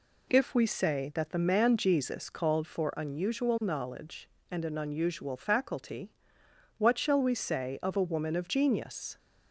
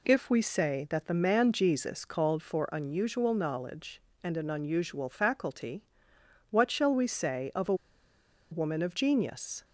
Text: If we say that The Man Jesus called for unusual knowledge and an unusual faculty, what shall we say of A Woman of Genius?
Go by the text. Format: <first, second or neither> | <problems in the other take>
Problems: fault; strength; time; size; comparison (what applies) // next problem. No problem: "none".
first | pauses between "A" and "Woman"; noticeable; at 7.7 s; 0.77 s long